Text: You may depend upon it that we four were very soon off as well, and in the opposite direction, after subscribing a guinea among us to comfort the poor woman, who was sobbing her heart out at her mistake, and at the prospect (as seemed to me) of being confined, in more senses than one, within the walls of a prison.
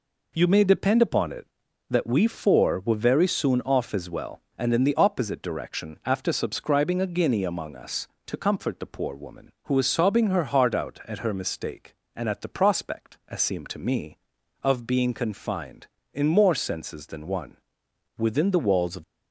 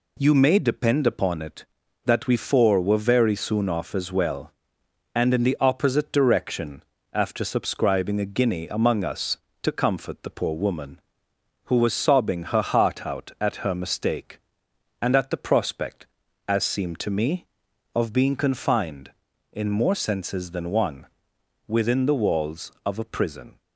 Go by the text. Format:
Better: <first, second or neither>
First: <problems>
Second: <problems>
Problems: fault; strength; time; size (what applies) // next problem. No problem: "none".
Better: second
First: stops before "a prison"; at 19.0 s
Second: none